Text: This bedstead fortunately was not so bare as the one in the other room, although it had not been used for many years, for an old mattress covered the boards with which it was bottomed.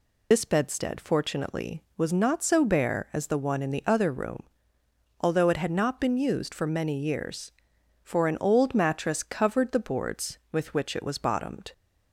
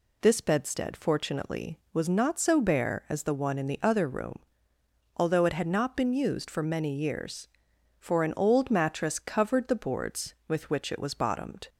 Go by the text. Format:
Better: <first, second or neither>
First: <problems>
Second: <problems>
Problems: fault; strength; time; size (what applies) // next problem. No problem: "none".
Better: second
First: loses the start of "This"; at 0.3 s; 45 ms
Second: none